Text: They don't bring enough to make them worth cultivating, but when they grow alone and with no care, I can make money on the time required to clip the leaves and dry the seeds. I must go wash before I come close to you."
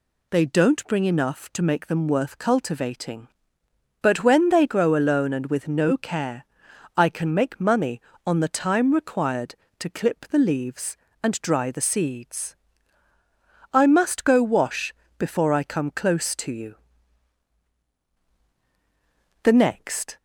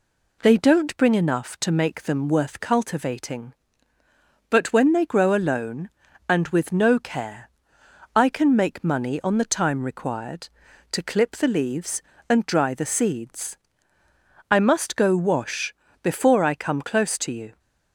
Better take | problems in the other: second | pauses between "wash" and "before"; slight; at 14.9 s; 0.24 s long; slight in the second // goes on to say "The next"; noticeable; from 19.4 s on; 0.74 s long

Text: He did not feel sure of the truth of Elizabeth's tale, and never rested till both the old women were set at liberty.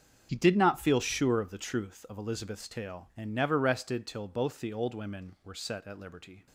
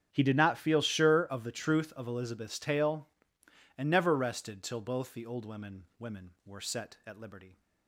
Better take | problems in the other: first | starts louder than the rest; strong; until 1.1 s; 8.5 dB; also in the first // says "women" twice; at 5.9 s

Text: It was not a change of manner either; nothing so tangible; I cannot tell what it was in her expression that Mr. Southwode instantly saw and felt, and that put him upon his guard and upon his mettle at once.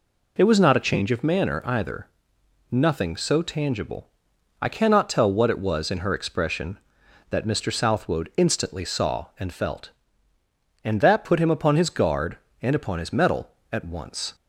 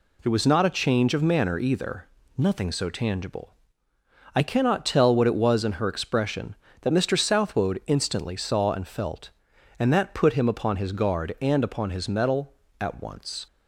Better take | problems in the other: neither | none

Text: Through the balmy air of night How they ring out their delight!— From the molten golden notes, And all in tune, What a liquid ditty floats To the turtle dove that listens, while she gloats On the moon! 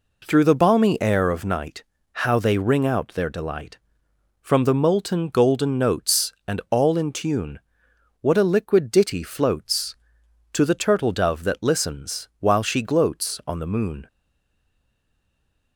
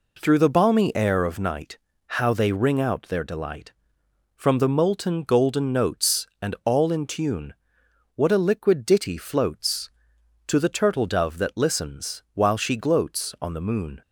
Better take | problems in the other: second | pauses between "night" and "How"; slight; at 1.8 s; 0.30 s long; slight in the second // stays silent after the last word; noticeable; from 14.0 s on; 1.7 s long

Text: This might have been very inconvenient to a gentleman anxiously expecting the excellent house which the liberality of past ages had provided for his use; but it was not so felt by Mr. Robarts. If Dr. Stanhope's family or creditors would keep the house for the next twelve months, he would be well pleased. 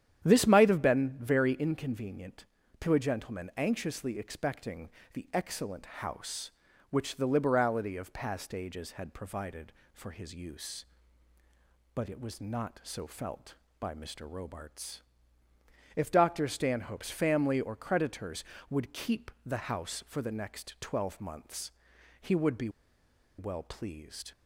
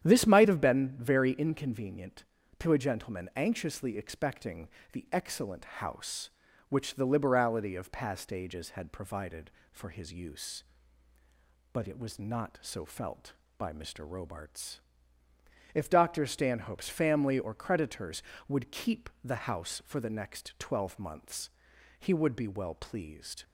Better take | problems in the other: second | starts louder than the rest; strong; until 1.2 s; 10 dB; strong in the second // pauses between "expecting" and "the"; slight; at 4.8 s; 0.26 s long; slight in the second // pauses between "keep" and "the"; slight; at 19.2 s; 0.16 s long; slight in the second // pauses between "be" and "well"; noticeable; at 22.6 s; 0.69 s long

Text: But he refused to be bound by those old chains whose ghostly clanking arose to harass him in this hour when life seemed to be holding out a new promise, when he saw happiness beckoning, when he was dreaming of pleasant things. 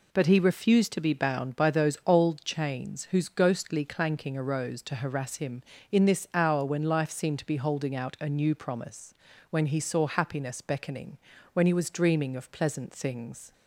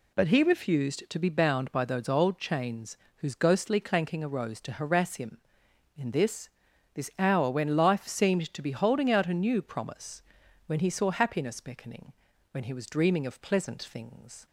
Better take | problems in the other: first | pauses between "chains" and "whose"; slight; at 2.9 s; 0.22 s long // says "this" twice; at 6.9 s

